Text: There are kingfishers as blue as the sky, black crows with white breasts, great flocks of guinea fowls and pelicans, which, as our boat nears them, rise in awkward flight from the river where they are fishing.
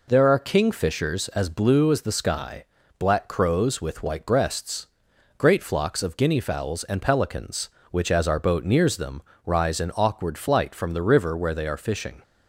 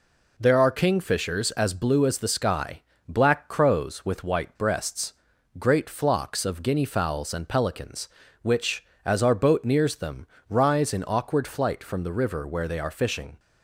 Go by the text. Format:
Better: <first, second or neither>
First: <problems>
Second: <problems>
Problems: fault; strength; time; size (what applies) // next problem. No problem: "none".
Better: neither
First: none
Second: none